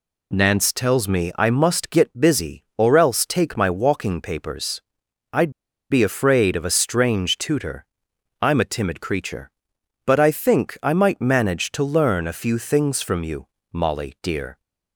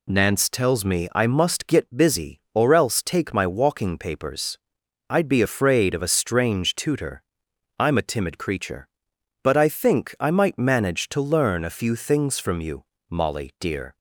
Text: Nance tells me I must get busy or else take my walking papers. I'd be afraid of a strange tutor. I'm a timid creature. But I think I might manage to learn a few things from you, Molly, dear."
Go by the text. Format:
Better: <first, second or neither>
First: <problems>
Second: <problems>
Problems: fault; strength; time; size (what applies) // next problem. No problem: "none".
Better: second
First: pauses between "I'd" and "be"; at 5.5 s; 0.38 s long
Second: none